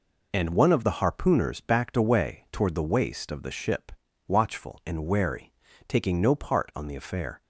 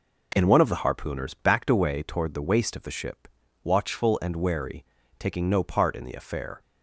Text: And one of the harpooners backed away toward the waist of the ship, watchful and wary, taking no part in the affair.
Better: second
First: says "on" for "in"; at 6.7 s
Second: none

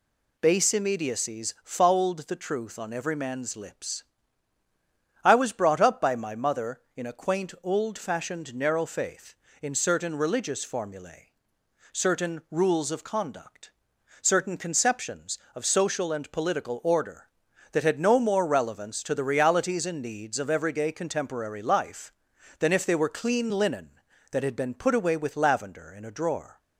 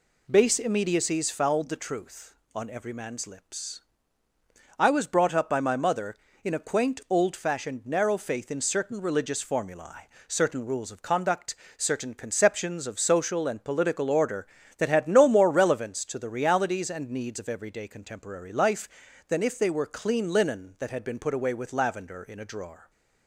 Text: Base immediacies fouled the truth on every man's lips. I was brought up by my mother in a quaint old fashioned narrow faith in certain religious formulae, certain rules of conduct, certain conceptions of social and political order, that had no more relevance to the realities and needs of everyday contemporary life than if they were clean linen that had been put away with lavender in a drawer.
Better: neither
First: none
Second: none

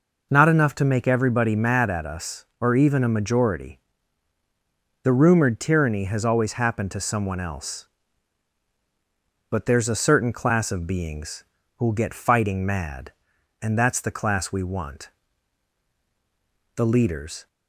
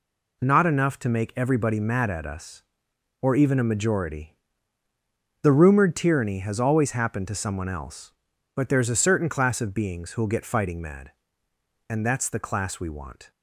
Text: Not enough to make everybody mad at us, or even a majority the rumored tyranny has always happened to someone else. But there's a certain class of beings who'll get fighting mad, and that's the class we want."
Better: second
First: pauses between "majority" and "the"; at 3.7 s; 1.2 s long // pauses between "beings" and "who'll"; slight; at 11.4 s; 0.32 s long // goes on to say "The leaders"; noticeable; from 16.7 s on; 0.72 s long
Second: pauses between "majority" and "the"; at 4.3 s; 1.0 s long

